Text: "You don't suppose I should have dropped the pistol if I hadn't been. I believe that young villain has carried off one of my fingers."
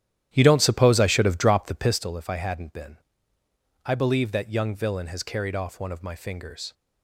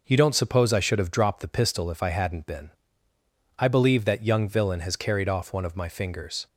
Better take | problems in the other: second | starts louder than the rest; strong; until 2.1 s; 11.5 dB

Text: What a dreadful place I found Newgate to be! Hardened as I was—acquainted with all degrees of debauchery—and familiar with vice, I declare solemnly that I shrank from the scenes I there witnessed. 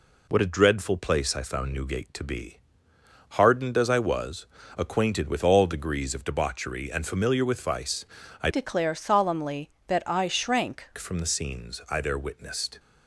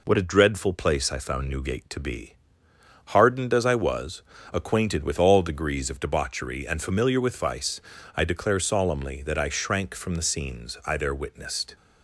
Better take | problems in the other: second | changes voice from "declare" to "shrank"; from 8.4 to 10.8 s; 2.4 s long

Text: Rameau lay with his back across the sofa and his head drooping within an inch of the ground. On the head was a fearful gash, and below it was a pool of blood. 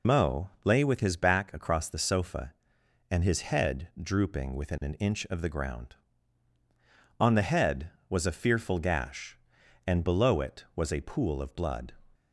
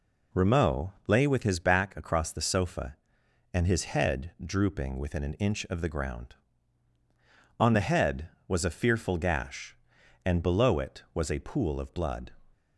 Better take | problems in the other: second | loses the start of "Rameau"; at 0.0 s; 145 ms

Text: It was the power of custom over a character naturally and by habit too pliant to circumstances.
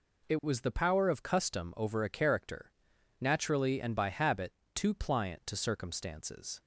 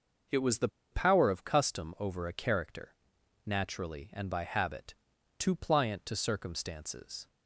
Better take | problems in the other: first | pauses between "the" and "power"; slight; at 0.6 s; 0.23 s long // pauses between "character" and "naturally"; noticeable; at 2.9 s; 0.50 s long; noticeable in the first // pauses between "habit" and "too"; at 4.9 s; 0.42 s long; slight in the first

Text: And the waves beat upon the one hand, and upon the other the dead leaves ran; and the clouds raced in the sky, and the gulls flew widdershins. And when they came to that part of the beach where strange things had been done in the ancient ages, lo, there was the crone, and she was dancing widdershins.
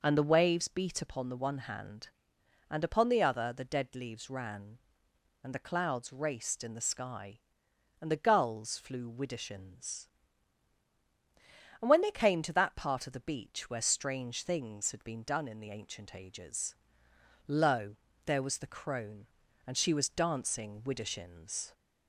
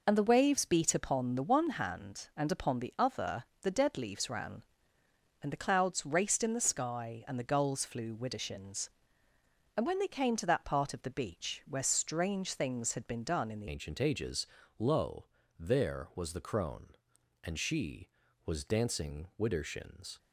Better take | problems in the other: first | pauses between "other" and "the"; slight; at 3.4 s; 0.16 s long // changes voice at "ancient"; from 13.6 s on; 6.5 s long

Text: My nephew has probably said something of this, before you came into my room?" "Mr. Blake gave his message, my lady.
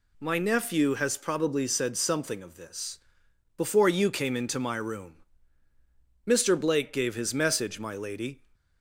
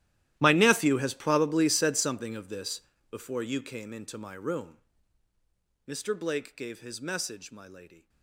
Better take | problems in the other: first | gets quieter; strong; throughout; 20 dB

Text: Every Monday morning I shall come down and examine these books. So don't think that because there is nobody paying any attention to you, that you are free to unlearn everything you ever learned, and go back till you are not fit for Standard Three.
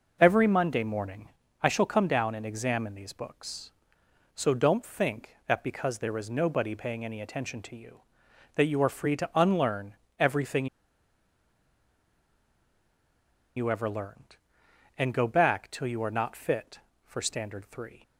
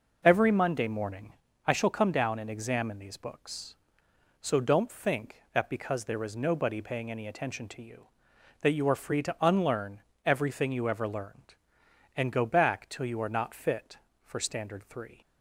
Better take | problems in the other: second | pauses between "morning" and "I"; slight; at 1.2 s; 0.34 s long; slight in the second // pauses between "unlearn" and "everything"; slight; at 9.9 s; 0.24 s long; slight in the second // pauses between "everything" and "you"; strong; at 10.6 s; 2.9 s long

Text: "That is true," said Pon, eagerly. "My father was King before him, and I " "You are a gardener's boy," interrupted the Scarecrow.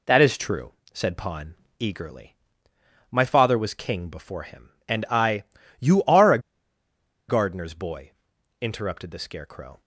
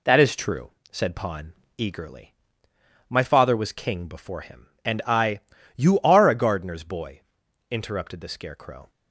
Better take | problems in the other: second | pauses between "a" and "gardener's"; noticeable; at 6.3 s; 0.89 s long

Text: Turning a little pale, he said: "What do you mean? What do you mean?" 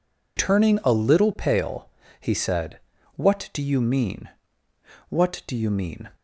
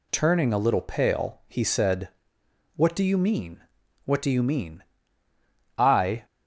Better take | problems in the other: first | goes on to say "I"; slight; from 5.7 s on; 0.48 s long

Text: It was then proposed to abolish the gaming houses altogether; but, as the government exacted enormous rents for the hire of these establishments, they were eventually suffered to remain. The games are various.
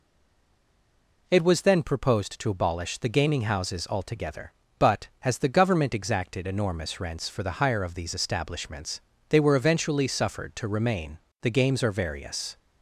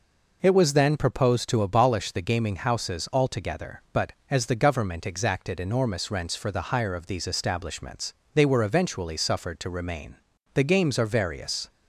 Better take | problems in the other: second | stays silent before the first word; noticeable; until 1.2 s; 1.2 s long

